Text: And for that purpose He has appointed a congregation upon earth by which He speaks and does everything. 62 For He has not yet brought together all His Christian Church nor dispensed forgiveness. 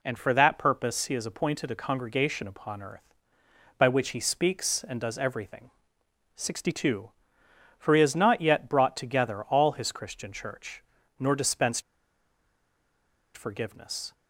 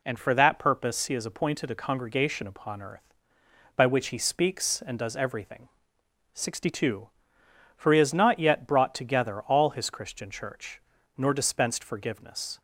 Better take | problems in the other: second | pauses between "Church" and "nor"; at 10.8 s; 0.38 s long; also in the second // pauses between "dispensed" and "forgiveness"; strong; at 11.8 s; 1.5 s long

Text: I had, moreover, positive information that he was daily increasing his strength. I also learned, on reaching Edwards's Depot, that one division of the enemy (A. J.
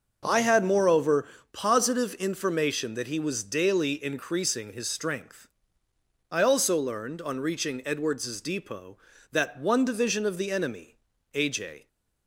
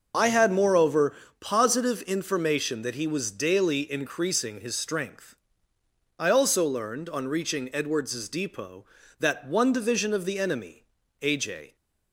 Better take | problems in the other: first | loses the start of "I"; at 0.1 s; 45 ms // starts louder than the rest; noticeable; until 1.4 s; 6 dB; also in the first

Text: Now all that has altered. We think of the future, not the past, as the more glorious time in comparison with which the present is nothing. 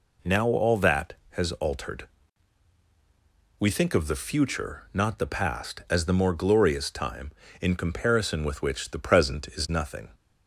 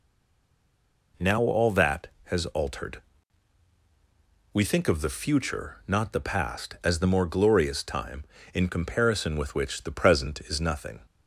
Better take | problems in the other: first | stays silent before the first word; noticeable; until 1.1 s; 1.1 s long

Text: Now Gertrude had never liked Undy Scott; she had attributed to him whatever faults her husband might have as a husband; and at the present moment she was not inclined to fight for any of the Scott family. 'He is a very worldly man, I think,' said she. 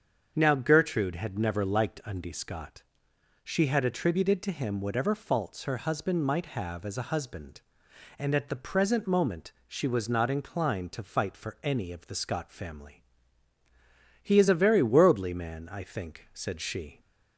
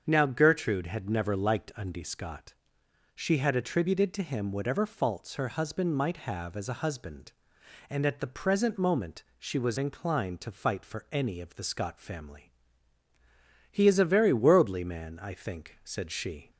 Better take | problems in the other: first | starts louder than the rest; until 1.0 s; 7 dB; also in the first // pauses between "moment" and "she"; slight; at 9.2 s; 0.16 s long; slight in the first // skips "not"; at 9.7 s

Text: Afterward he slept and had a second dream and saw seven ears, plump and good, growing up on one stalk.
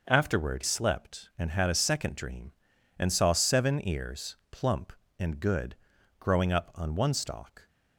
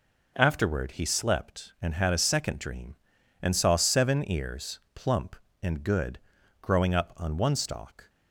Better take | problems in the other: second | skips "he"; at 0.6 s

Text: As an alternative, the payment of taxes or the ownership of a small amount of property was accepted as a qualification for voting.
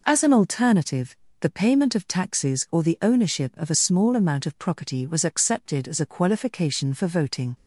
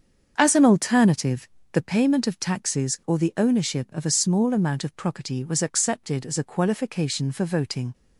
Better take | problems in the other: first | starts louder than the rest; strong; until 1.9 s; 7 dB

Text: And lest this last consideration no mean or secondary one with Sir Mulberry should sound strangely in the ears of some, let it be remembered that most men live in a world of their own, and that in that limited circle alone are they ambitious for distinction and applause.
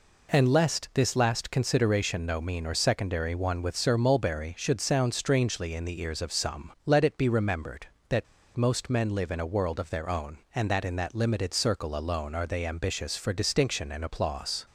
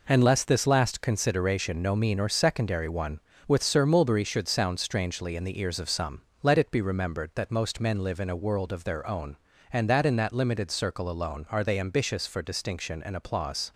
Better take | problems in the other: second | pauses between "that" and "most"; slight; at 8.2 s; 0.32 s long

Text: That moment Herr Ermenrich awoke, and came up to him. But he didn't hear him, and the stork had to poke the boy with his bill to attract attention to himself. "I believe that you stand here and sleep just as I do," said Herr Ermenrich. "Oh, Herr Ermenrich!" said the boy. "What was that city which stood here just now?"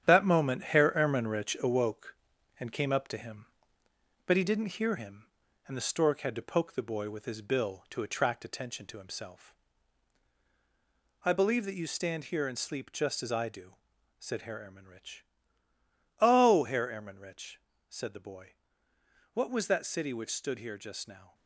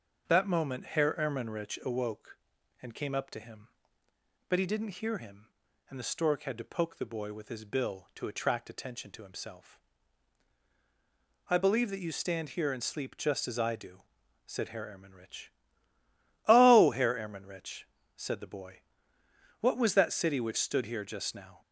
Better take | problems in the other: second | gets quieter; throughout; 7 dB // starts louder than the rest; strong; until 1.1 s; 9.5 dB; noticeable in the second

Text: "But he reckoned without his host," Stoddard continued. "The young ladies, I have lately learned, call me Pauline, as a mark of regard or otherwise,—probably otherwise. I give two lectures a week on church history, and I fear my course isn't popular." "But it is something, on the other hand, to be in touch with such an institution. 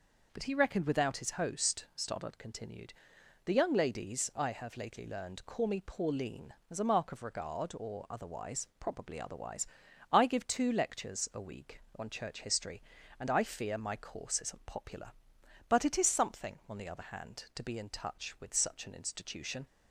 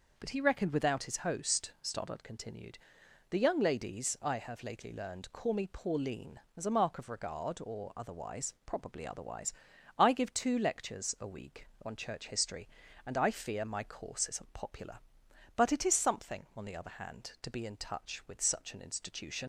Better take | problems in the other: first | leaves "institution" unfinished; at 19.4 s; 50 ms

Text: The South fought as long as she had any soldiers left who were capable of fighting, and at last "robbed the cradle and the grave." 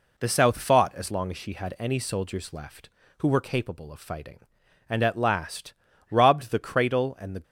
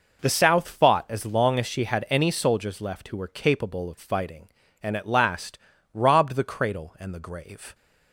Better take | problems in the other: second | pauses between "last" and "robbed"; slight; at 5.7 s; 0.36 s long; also in the second // stops before "grave"; at 7.4 s

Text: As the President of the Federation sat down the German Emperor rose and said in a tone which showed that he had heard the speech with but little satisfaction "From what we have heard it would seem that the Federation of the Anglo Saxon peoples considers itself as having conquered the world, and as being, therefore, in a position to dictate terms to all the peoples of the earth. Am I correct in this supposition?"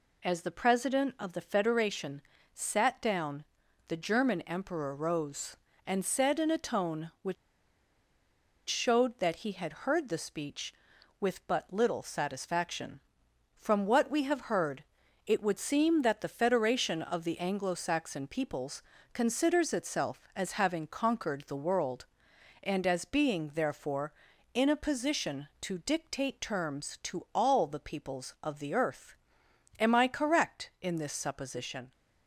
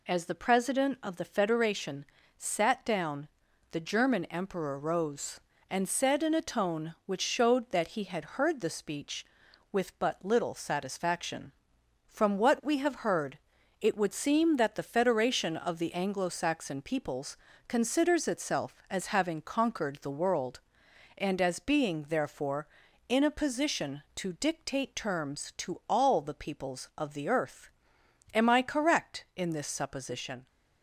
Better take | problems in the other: second | pauses between "Federation" and "sat"; slight; at 2.2 s; 0.32 s long; slight in the second // pauses between "down" and "the"; at 3.4 s; 0.42 s long; also in the second // pauses between "which" and "showed"; strong; at 7.3 s; 1.3 s long // pauses between "heard" and "it"; at 14.8 s; 0.42 s long; also in the second // pauses between "peoples" and "considers"; slight; at 18.8 s; 0.30 s long; slight in the second

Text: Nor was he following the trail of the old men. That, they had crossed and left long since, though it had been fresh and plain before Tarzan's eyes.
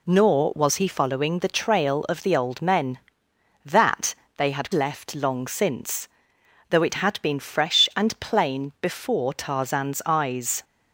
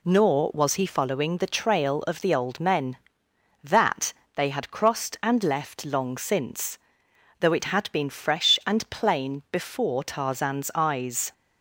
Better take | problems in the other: second | skips "crossed and"; at 4.7 s

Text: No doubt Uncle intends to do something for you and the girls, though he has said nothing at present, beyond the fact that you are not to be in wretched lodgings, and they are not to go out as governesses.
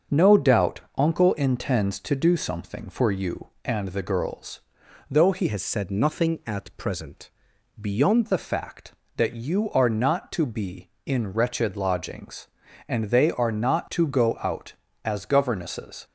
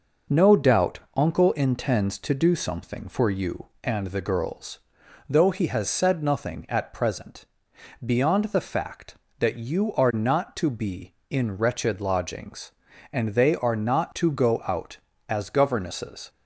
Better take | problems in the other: second | starts louder than the rest; until 1.2 s; 6.5 dB; noticeable in the second // pauses between "doubt" and "Uncle"; slight; at 0.8 s; 0.16 s long; slight in the second // changes voice from "has" to "beyond"; from 5.4 to 8.2 s; 2.8 s long

